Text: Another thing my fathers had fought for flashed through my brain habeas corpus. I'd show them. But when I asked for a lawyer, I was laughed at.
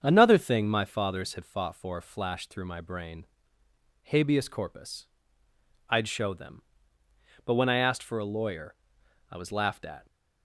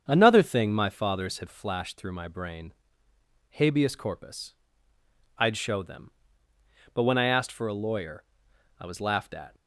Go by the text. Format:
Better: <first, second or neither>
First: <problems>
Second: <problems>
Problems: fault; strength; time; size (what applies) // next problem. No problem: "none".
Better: first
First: starts louder than the rest; strong; until 1.0 s; 7.5 dB // pauses between "brain" and "habeas"; noticeable; at 3.2 s; 0.78 s long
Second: starts louder than the rest; strong; until 1.0 s; 7.5 dB // skips "fought for"; at 1.4 s // pauses between "brain" and "habeas"; noticeable; at 2.7 s; 0.78 s long